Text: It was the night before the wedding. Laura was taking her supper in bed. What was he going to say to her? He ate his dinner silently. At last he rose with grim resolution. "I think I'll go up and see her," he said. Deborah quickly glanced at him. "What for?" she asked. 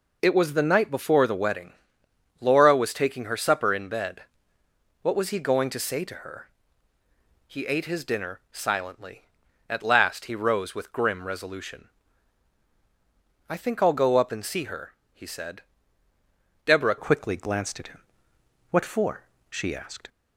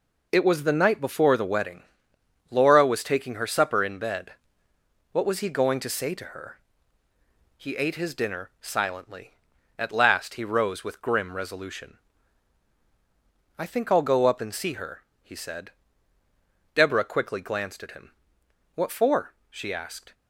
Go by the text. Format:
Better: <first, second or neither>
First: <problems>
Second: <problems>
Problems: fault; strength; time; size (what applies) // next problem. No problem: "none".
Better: second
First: changes voice at "quickly"; from 16.9 s on; 3.1 s long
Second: none